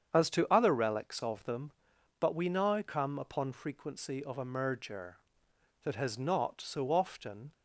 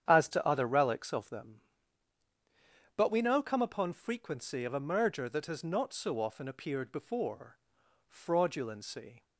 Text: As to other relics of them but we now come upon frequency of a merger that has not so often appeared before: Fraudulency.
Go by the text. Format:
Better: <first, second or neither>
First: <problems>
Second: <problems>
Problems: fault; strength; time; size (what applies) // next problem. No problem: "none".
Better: second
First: starts louder than the rest; strong; until 1.1 s; 8 dB // stops before "appeared before Fraudulency"; at 7.5 s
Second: starts louder than the rest; strong; until 1.1 s; 9 dB